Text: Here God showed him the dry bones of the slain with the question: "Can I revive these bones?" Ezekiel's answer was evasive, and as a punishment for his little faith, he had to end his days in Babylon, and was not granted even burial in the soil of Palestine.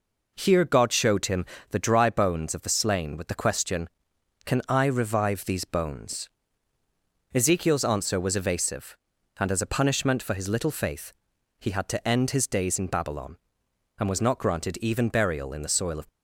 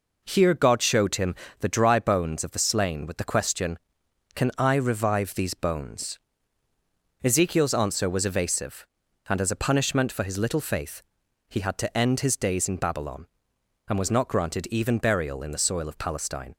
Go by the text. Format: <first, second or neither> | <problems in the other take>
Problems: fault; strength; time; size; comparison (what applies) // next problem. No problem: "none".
second | pauses between "him" and "the"; slight; at 1.4 s; 0.24 s long; slight in the second // stops before "Palestine"; at 16.0 s